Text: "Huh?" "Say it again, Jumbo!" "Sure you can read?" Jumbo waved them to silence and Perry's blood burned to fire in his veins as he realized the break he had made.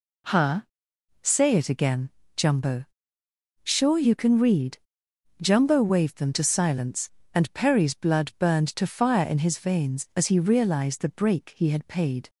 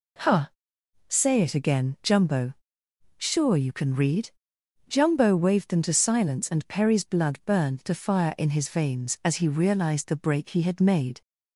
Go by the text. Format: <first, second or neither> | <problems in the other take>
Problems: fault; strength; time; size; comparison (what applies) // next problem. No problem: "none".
second | says "paid" for "made"; at 11.8 s